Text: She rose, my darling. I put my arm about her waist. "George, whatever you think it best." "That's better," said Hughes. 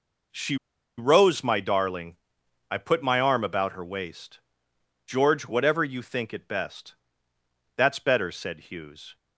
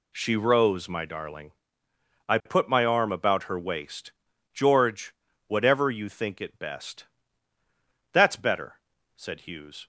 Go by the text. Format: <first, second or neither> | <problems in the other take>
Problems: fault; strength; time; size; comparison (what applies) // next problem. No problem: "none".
second | pauses between "She" and "rose"; at 0.5 s; 0.42 s long